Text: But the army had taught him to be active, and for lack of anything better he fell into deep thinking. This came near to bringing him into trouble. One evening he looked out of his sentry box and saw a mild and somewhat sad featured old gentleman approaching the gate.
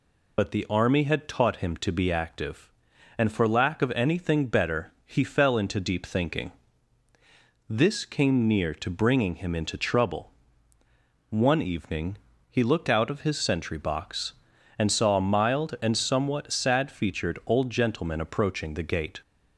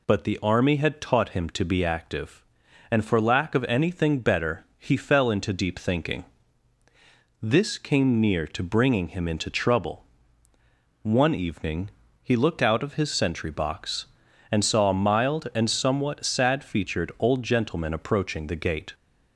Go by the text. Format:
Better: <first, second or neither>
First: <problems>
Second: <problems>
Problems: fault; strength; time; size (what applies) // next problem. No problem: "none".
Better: second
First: loses the start of "But"; at 0.3 s; 50 ms // pauses between "evening" and "he"; slight; at 12.1 s; 0.32 s long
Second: pauses between "evening" and "he"; slight; at 11.9 s; 0.32 s long